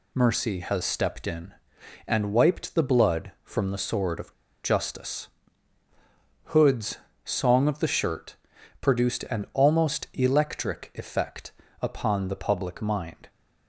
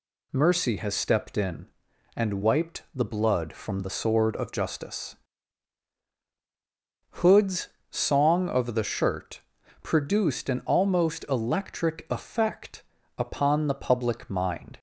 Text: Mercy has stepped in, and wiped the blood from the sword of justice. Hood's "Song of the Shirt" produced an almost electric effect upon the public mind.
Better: second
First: pauses between "of" and "justice"; slight; at 4.3 s; 0.30 s long // pauses between "Hood's" and "Song"; slight; at 6.9 s; 0.28 s long // pauses between "Shirt" and "produced"; at 8.3 s; 0.44 s long // pauses between "effect" and "upon"; slight; at 11.5 s; 0.30 s long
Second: pauses between "Hood's" and "Song"; slight; at 7.6 s; 0.22 s long // pauses between "Shirt" and "produced"; at 9.4 s; 0.42 s long // pauses between "effect" and "upon"; slight; at 12.8 s; 0.34 s long

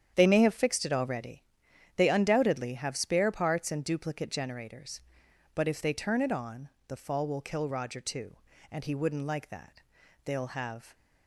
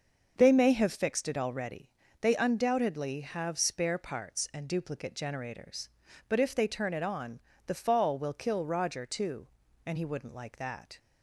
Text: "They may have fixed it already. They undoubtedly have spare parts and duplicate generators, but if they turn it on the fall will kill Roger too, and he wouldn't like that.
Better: second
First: starts louder than the rest; strong; until 1.1 s; 9 dB // pauses between "on" and "the"; slight; at 6.6 s; 0.20 s long // goes on to say "They'll have"; noticeable; from 10.2 s on; 0.70 s long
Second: starts louder than the rest; until 1.3 s; 6.5 dB // pauses between "on" and "the"; slight; at 7.3 s; 0.28 s long

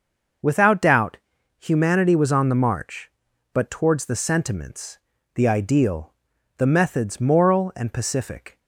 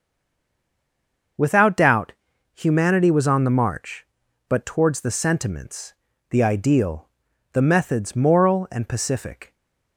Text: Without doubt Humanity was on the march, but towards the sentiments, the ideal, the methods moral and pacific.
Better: first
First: pauses between "doubt" and "Humanity"; at 1.1 s; 0.40 s long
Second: stays silent before the first word; noticeable; until 1.3 s; 1.3 s long // pauses between "doubt" and "Humanity"; at 2.1 s; 0.40 s long // stays silent after the last word; slight; from 9.4 s on; 0.5 s long

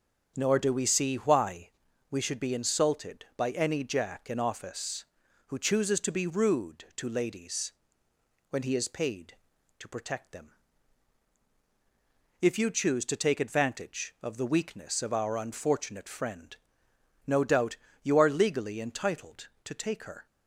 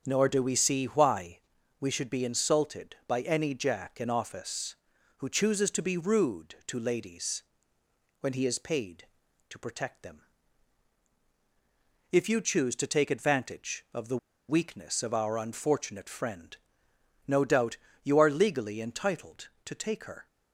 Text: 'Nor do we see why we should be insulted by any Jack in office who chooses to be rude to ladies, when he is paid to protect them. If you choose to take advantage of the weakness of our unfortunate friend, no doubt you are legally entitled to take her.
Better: first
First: starts louder than the rest; until 1.3 s; 6.5 dB // pauses between "why" and "we"; at 1.6 s; 0.40 s long // pauses between "doubt" and "you"; slight; at 17.7 s; 0.26 s long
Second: starts louder than the rest; until 1.0 s; 6.5 dB // pauses between "why" and "we"; at 1.3 s; 0.40 s long // pauses between "the" and "weakness"; slight; at 14.1 s; 0.31 s long // pauses between "doubt" and "you"; slight; at 17.7 s; 0.26 s long

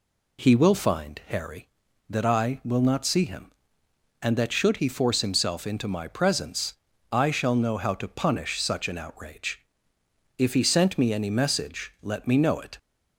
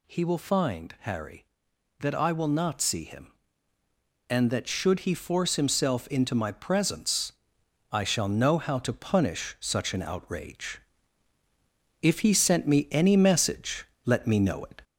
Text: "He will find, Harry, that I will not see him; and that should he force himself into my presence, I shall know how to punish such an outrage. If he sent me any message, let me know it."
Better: first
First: none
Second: gets louder; slight; throughout; 2.5 dB

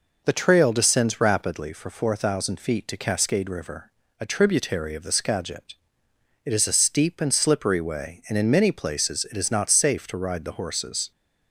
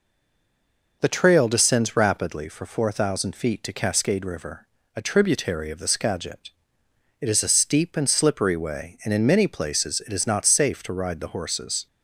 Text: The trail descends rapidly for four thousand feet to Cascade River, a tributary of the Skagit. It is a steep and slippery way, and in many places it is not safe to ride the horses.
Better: first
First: none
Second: stays silent before the first word; until 1.0 s; 1.0 s long

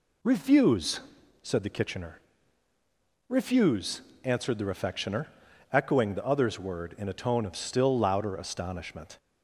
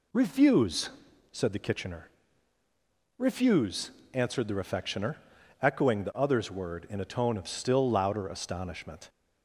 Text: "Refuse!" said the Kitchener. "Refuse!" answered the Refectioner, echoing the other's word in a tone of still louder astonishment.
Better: neither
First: none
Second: none

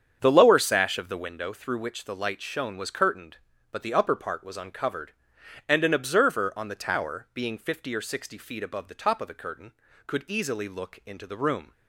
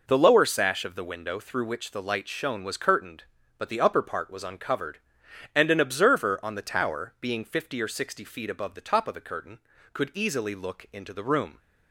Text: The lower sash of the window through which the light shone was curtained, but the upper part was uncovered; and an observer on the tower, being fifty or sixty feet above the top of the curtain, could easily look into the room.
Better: second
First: starts louder than the rest; strong; until 1.3 s; 7.5 dB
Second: none

